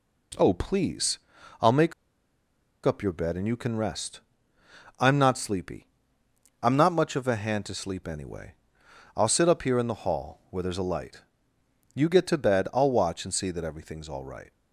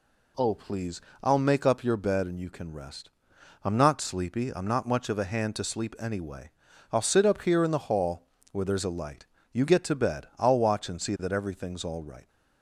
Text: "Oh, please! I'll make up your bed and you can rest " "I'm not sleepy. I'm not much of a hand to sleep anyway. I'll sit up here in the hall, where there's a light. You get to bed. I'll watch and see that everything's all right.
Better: second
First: pauses between "make" and "up"; noticeable; at 1.9 s; 0.91 s long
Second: none

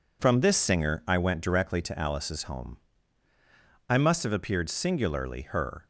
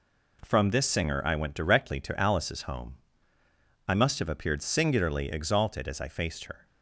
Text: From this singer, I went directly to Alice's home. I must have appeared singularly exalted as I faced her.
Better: second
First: skips "exalted as I faced"; at 5.4 s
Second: none

